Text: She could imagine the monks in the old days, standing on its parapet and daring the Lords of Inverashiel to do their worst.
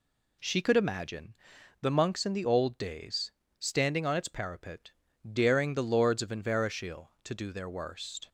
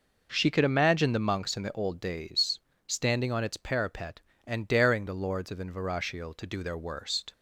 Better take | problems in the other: second | pauses between "imagine" and "the"; noticeable; at 1.3 s; 0.46 s long // skips "and"; at 5.1 s

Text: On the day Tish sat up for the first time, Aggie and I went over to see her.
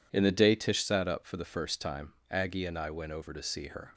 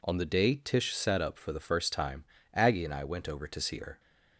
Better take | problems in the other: second | says "In" for "On"; at 0.1 s

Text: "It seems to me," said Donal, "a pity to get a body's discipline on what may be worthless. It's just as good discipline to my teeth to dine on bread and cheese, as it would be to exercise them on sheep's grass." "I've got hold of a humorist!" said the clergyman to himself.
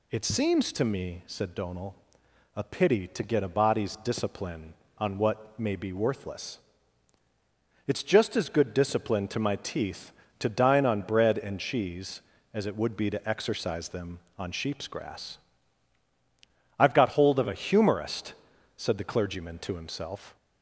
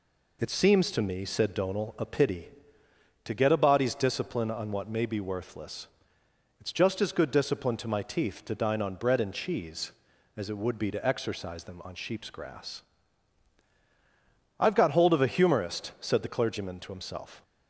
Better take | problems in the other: neither | none

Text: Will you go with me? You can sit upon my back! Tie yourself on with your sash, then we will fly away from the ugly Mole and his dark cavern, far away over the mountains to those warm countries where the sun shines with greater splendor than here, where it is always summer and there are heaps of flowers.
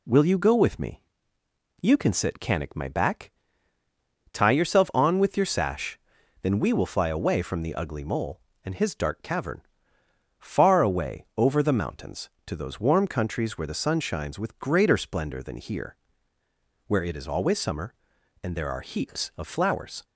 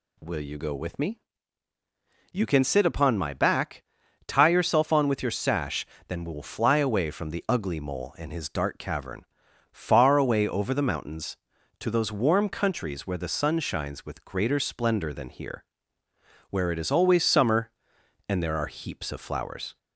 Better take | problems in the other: second | says "canic" for "upon"; at 2.3 s

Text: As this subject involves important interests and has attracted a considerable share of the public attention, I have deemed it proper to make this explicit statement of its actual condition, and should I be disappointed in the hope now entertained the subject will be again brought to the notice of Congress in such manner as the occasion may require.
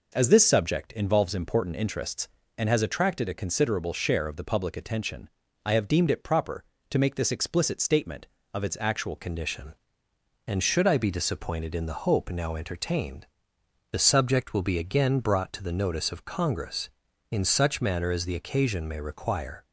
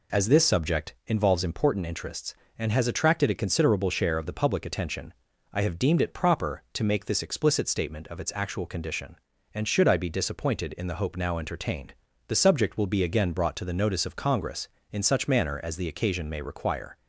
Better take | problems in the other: second | changes voice at "condition"; from 9.1 s on; 10.5 s long // pauses between "entertained" and "the"; noticeable; at 13.2 s; 0.64 s long; slight in the second

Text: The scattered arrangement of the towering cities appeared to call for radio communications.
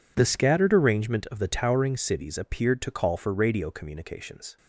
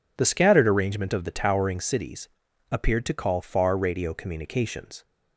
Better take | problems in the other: first | pauses between "cities" and "appeared"; at 2.2 s; 0.42 s long // says "far" for "for"; at 3.4 s

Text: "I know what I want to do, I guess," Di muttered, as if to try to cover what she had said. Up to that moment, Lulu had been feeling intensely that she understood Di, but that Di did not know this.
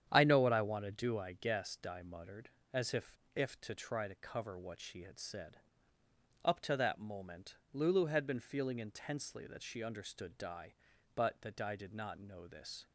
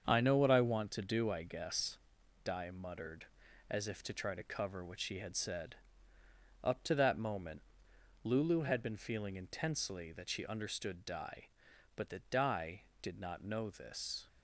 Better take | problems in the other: second | starts louder than the rest; strong; until 1.1 s; 9 dB; also in the second // says "if" twice; at 3.3 s

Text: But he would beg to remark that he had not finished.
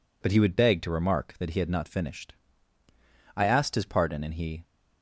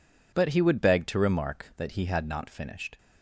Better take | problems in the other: second | goes on to say "I asked his pardon and he"; noticeable; from 3.3 s on; 1.2 s long

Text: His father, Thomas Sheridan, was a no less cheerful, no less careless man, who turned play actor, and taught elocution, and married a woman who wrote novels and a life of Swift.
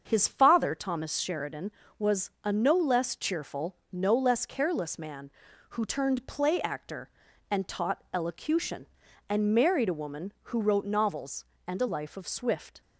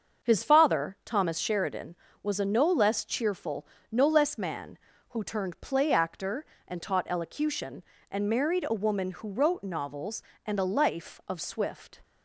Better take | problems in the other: first | starts louder than the rest; until 1.3 s; 6.5 dB; also in the first // skips "careless"; at 4.3 s

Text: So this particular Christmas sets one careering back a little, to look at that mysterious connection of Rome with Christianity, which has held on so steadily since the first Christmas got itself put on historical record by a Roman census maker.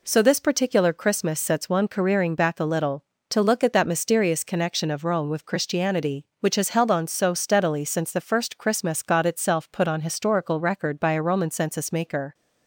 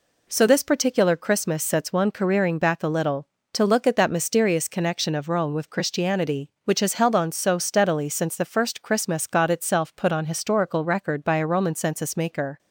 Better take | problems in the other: neither | none

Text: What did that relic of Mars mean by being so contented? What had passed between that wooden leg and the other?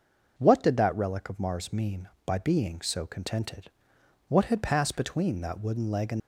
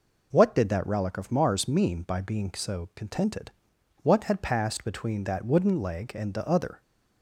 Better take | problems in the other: second | stops before "the other"; at 6.1 s

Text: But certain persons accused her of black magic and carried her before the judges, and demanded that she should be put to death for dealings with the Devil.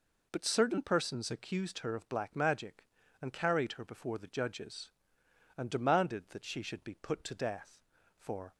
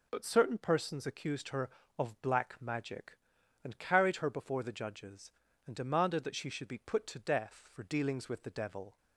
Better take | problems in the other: second | stops before "dealings with the Devil"; at 8.5 s

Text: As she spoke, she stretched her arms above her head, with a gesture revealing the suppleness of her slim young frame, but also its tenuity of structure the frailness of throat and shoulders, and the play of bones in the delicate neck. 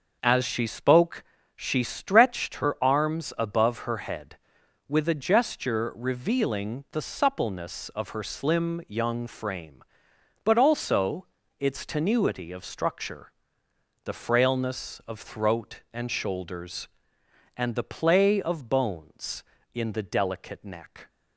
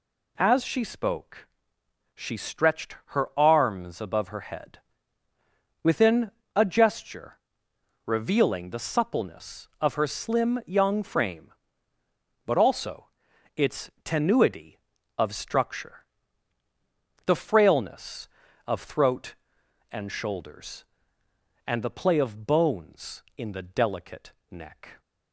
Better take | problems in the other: first | says "within" for "with"; at 5.8 s // pauses between "gesture" and "revealing"; noticeable; at 7.3 s; 0.66 s long // pauses between "also" and "its"; noticeable; at 13.0 s; 0.48 s long; slight in the first // pauses between "structure" and "the"; at 16.0 s; 1.2 s long; noticeable in the first // pauses between "delicate" and "neck"; slight; at 24.3 s; 0.18 s long

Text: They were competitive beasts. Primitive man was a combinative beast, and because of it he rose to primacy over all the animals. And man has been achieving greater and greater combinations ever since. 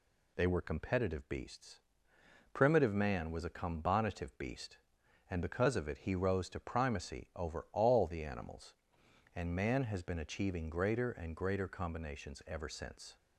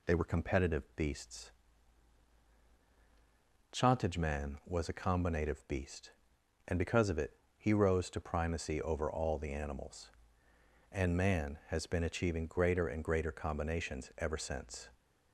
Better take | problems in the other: first | says "Chantage" for "Primitive"; at 3.7 s // pauses between "it" and "he"; slight; at 7.3 s; 0.26 s long

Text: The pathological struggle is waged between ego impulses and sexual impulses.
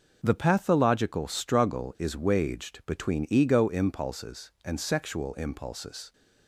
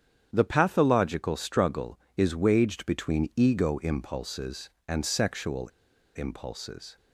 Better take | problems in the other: first | starts louder than the rest; strong; until 1.3 s; 9 dB // pauses between "sexual" and "impulses"; noticeable; at 5.6 s; 0.46 s long

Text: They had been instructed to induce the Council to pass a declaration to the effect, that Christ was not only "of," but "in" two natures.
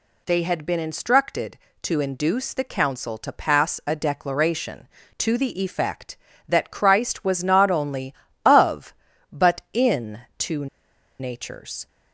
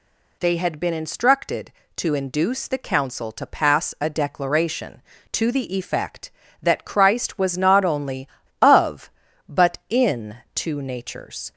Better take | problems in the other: second | pauses between "in" and "two"; slight; at 10.2 s; 0.16 s long; slight in the second // pauses between "two" and "natures"; noticeable; at 10.6 s; 0.53 s long

